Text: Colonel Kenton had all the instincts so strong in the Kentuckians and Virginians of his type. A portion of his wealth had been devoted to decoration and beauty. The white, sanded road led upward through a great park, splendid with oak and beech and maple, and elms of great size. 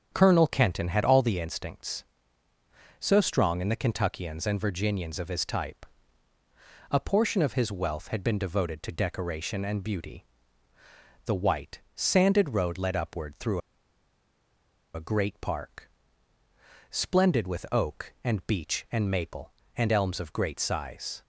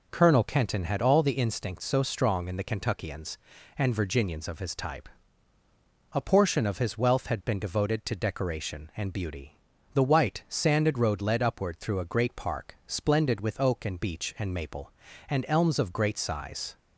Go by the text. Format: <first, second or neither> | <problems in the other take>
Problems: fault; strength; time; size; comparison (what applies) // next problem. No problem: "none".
second | starts louder than the rest; strong; until 1.1 s; 8 dB // pauses between "through" and "a"; strong; at 13.5 s; 1.3 s long